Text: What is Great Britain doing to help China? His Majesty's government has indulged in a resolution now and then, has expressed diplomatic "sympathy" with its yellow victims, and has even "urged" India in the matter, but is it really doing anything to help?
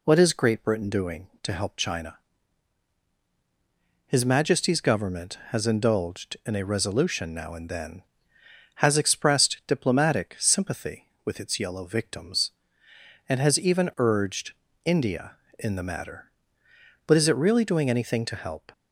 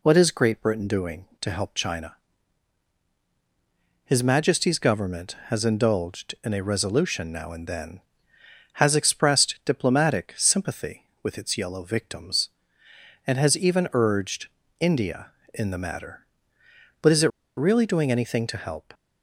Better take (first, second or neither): first